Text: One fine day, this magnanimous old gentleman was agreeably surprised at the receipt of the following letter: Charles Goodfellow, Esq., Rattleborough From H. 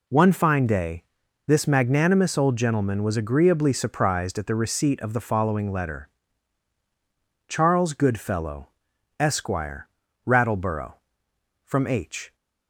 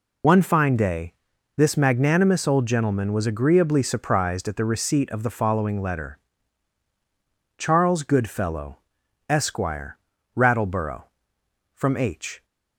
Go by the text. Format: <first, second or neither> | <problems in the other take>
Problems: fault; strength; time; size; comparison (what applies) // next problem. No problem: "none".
first | loses the start of "One"; at 0.2 s; 60 ms